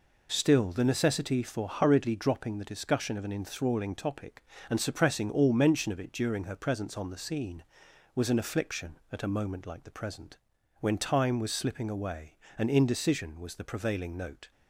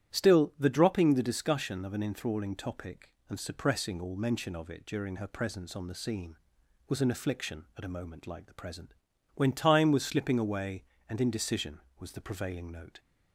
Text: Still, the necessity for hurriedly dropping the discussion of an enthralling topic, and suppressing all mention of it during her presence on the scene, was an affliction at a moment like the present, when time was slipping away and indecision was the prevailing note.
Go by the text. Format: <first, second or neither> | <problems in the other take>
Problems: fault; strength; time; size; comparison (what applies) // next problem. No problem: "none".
first | starts louder than the rest; strong; until 1.2 s; 11 dB // skips "necessity for hurriedly"; at 0.6 s